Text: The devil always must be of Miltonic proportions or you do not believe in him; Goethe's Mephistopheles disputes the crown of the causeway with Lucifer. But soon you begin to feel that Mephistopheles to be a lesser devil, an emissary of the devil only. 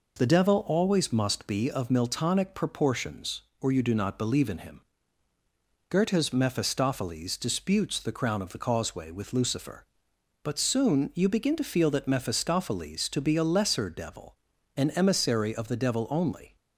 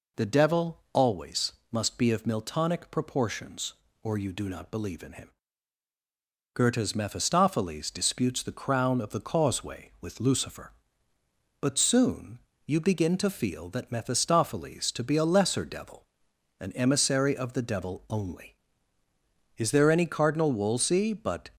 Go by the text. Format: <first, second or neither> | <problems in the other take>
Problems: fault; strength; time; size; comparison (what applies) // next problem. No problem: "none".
first | pauses between "always" and "must"; slight; at 1.5 s; 0.20 s long // pauses between "soon" and "you"; slight; at 12.3 s; 0.26 s long // goes on to say "Is there any Cardinal Wolsey but"; strong; from 19.5 s on; 1.9 s long